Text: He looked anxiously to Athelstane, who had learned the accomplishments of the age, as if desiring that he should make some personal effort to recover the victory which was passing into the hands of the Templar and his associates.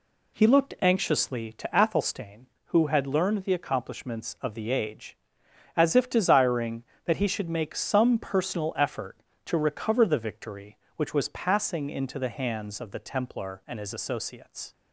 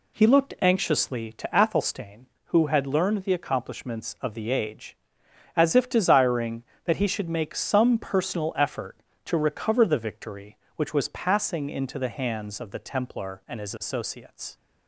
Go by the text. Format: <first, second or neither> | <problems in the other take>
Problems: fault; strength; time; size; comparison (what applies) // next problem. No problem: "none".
neither | none